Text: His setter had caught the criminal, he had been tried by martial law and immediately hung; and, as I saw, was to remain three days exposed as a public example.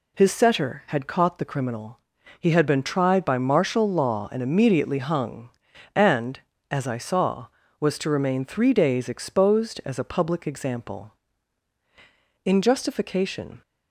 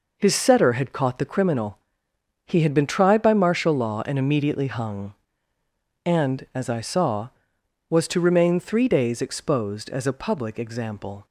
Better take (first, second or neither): second